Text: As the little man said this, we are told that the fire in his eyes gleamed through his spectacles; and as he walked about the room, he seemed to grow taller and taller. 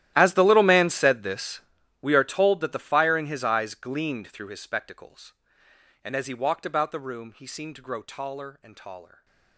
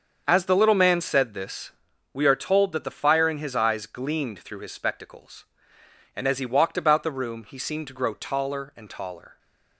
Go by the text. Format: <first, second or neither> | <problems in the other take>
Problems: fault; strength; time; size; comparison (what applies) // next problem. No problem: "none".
second | gets quieter; strong; throughout; 20.5 dB // starts louder than the rest; strong; until 1.1 s; 14 dB; also in the second